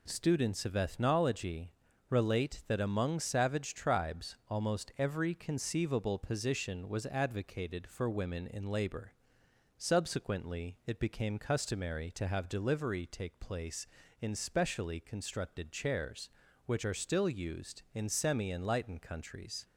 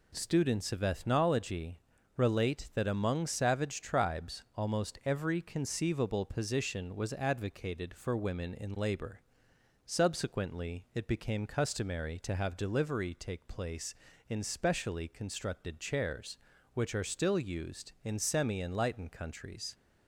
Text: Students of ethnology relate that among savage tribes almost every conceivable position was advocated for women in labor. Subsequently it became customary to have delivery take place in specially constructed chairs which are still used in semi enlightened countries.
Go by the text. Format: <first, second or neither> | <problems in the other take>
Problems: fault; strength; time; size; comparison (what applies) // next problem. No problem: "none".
neither | pauses between "ethnology" and "relate"; slight; the same in both